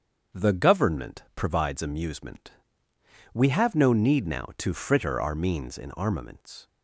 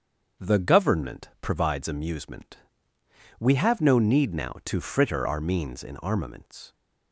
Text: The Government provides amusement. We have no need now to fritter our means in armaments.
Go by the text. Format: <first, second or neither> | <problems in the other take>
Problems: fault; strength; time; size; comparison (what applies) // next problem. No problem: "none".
neither | starts louder than the rest; the same in both